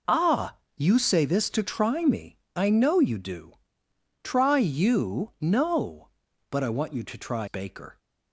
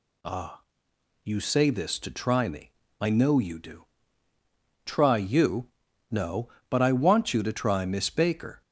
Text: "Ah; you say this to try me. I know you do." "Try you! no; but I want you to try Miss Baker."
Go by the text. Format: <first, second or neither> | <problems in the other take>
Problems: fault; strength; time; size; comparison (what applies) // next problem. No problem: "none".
second | skips "Miss"; at 7.4 s